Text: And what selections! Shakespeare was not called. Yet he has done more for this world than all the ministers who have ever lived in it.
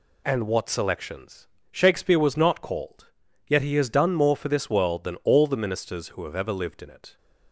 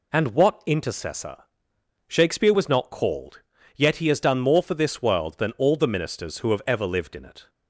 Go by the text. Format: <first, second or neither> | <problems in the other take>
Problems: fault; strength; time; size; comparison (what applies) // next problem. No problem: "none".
first | says "intercessor" for "selections"; at 0.6 s